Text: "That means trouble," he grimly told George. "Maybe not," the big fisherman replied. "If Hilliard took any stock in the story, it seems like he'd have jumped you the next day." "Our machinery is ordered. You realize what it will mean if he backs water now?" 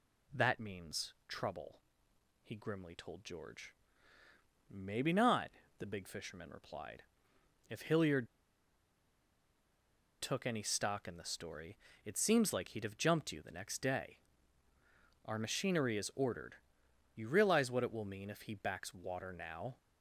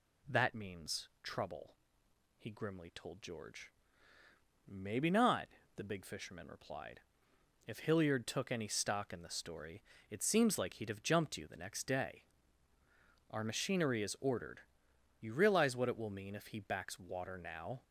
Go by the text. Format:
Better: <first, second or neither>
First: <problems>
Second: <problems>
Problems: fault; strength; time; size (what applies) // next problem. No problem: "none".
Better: second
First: pauses between "Hilliard" and "took"; strong; at 8.2 s; 1.9 s long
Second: none